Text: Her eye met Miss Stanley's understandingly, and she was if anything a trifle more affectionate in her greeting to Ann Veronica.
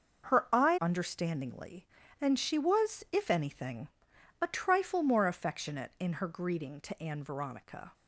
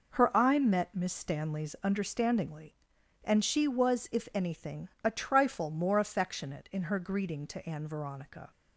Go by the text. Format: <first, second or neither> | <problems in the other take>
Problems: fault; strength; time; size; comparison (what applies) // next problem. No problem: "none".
second | starts louder than the rest; until 1.3 s; 6.5 dB // skips "met Miss Stanley's"; at 0.7 s // pauses between "anything" and "a"; noticeable; at 3.8 s; 0.56 s long